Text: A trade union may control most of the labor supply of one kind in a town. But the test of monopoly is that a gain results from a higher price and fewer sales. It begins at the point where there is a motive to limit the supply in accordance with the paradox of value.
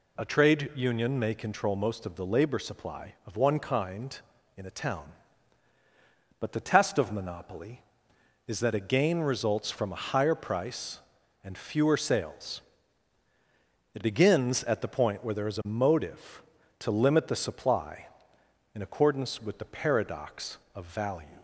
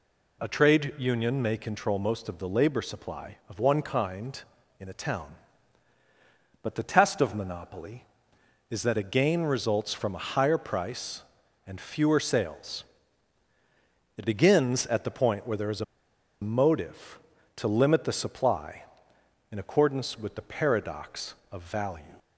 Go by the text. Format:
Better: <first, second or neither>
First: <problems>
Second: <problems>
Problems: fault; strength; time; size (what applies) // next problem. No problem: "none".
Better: first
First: none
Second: pauses between "a" and "motive"; noticeable; at 15.8 s; 0.57 s long